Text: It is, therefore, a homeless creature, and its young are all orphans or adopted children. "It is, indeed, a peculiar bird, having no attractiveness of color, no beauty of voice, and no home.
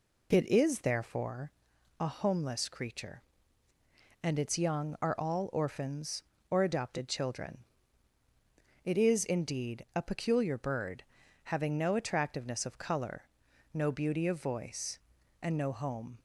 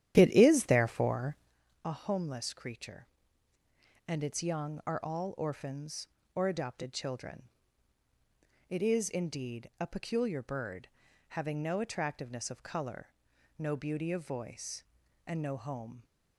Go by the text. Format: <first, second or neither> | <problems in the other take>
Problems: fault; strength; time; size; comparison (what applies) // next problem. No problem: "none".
first | starts louder than the rest; strong; until 1.6 s; 11.5 dB